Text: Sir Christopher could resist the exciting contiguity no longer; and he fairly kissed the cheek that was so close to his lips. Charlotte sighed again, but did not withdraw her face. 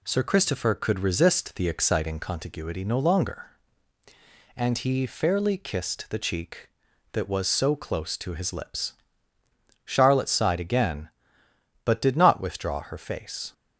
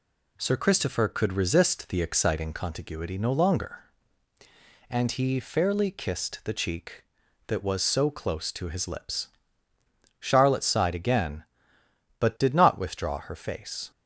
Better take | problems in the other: neither | none

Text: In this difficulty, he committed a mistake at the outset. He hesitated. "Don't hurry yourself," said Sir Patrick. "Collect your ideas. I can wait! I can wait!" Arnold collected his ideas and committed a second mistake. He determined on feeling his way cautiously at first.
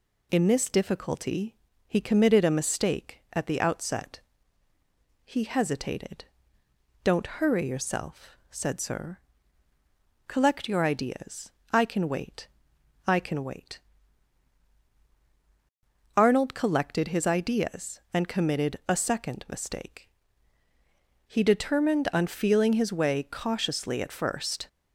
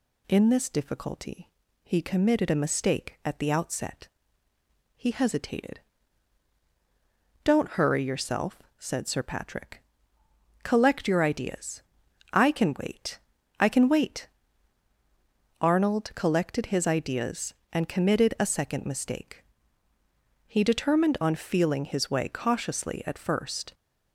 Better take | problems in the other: second | skips "Patrick"; at 9.7 s

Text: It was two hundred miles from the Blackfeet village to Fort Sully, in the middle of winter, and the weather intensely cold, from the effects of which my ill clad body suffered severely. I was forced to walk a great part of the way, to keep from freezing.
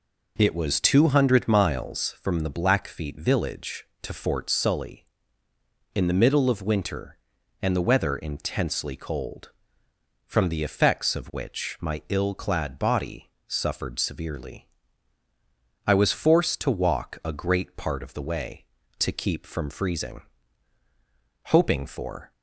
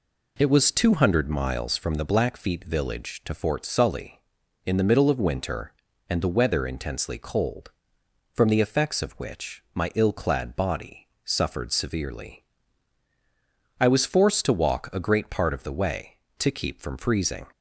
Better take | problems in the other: second | pauses between "body" and "suffered"; slight; at 13.2 s; 0.18 s long; slight in the second // goes on to say "Hoping for"; noticeable; from 21.4 s on; 0.84 s long

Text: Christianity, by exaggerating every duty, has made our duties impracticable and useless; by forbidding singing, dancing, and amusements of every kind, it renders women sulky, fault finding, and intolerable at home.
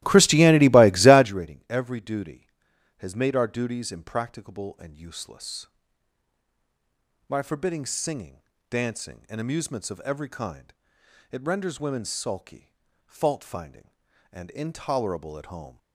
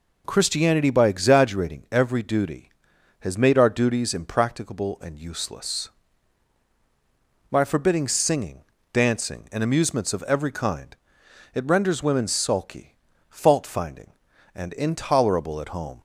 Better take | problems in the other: second | starts louder than the rest; strong; until 1.4 s; 15.5 dB

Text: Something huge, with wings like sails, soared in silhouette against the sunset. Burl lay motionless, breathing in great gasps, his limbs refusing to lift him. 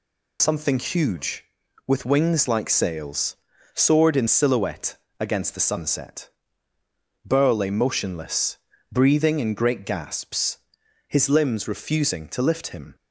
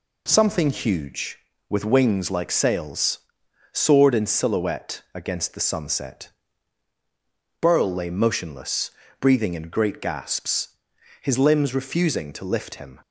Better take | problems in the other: second | loses the start of "Something"; at 0.3 s; 45 ms // pauses between "silhouette" and "against"; slight; at 4.9 s; 0.22 s long

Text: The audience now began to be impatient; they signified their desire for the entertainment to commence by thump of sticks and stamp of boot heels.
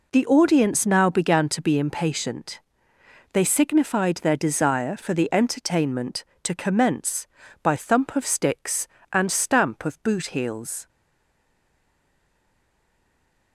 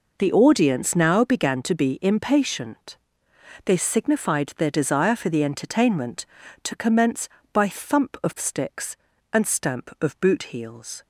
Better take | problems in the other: second | stays silent after the last word; strong; from 10.8 s on; 2.7 s long

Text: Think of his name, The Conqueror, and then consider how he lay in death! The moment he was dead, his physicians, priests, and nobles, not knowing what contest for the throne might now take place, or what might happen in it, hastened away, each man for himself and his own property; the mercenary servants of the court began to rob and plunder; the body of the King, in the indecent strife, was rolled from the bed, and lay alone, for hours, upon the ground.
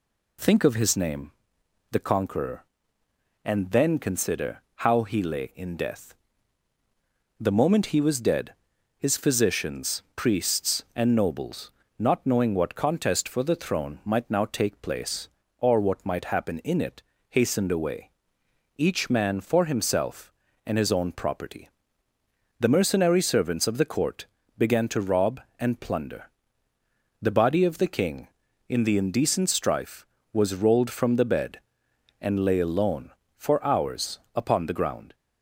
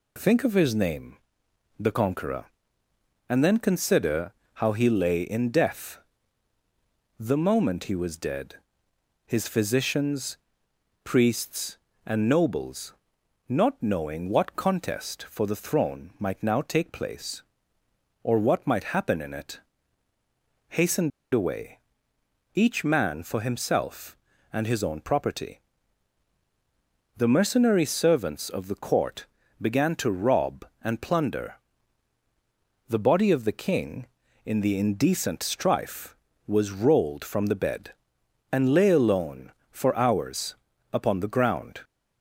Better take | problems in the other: first | pauses between "consider" and "how"; slight; at 4.3 s; 0.22 s long; slight in the first // pauses between "hastened" and "away"; slight; at 21.1 s; 0.24 s long // pauses between "court" and "began"; slight; at 29.2 s; 0.36 s long; slight in the first

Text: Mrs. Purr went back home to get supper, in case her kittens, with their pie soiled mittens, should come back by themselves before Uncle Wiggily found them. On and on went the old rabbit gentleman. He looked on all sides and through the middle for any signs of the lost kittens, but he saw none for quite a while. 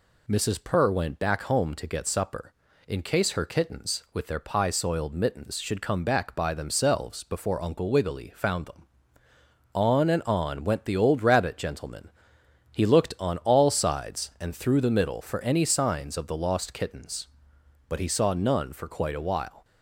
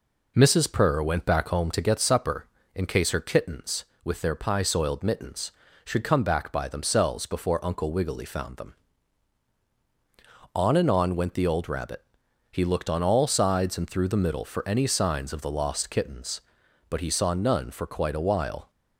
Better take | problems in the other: first | skips "gentleman"; at 12.2 s

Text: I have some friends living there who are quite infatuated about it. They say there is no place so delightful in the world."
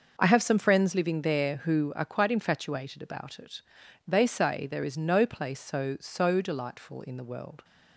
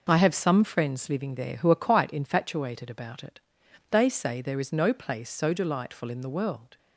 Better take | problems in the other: second | starts louder than the rest; noticeable; until 1.1 s; 6 dB // says "so" twice; at 5.9 s

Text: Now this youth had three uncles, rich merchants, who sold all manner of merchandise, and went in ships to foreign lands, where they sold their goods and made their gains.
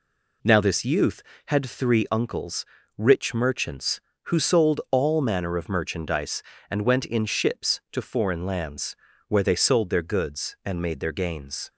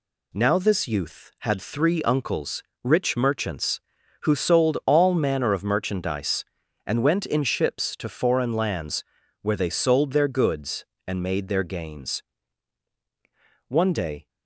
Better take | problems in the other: first | goes on to say "One day"; from 13.6 s on; 0.60 s long

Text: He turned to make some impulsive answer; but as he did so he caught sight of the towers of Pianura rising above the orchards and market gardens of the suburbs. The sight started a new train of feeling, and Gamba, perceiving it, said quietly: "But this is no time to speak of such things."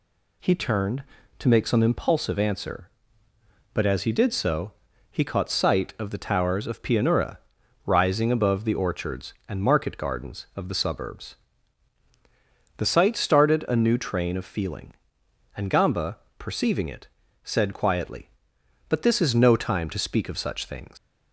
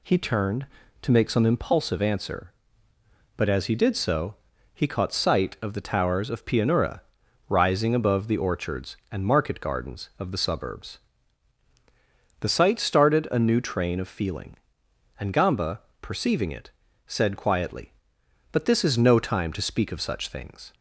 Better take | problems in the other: second | pauses between "so" and "he"; at 4.7 s; 0.38 s long; also in the second // pauses between "Pianura" and "rising"; noticeable; at 7.3 s; 0.46 s long; noticeable in the second // leaves "things" unfinished; at 20.9 s; 135 ms

